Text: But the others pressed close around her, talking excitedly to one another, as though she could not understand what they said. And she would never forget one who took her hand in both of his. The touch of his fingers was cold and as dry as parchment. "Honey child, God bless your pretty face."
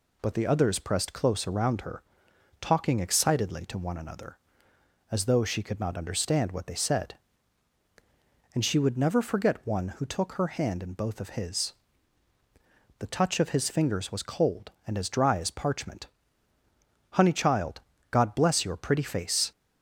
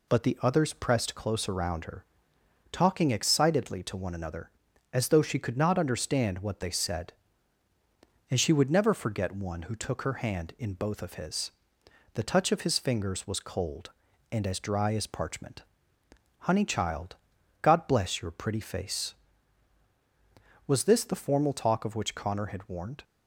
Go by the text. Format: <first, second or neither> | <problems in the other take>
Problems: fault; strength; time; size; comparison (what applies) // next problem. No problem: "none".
first | goes on to say "Was this the formal talk of which Connor had warned"; strong; from 20.6 s on; 2.3 s long